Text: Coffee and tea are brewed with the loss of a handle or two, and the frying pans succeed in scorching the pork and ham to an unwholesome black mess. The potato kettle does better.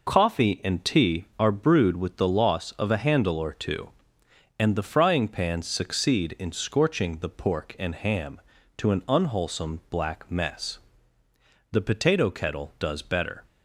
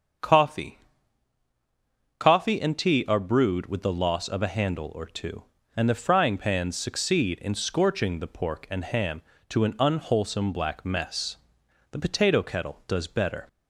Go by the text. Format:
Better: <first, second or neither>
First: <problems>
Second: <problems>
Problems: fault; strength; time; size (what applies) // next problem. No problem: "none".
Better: first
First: none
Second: starts louder than the rest; until 2.6 s; 7 dB // says "Coffee" twice; at 2.1 s